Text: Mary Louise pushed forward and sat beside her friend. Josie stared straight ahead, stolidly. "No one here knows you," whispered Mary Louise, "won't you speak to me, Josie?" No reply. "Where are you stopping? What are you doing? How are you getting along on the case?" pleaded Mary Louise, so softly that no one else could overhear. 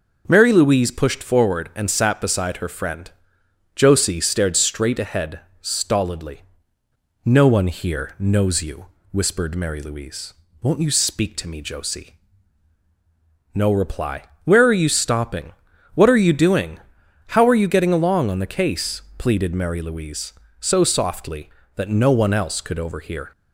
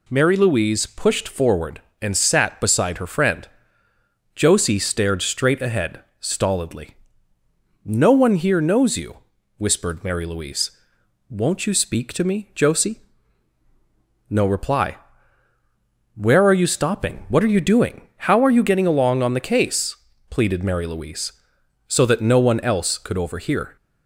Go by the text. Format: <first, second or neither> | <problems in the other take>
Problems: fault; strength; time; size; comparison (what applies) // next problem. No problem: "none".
first | skips "softly"; at 22.0 s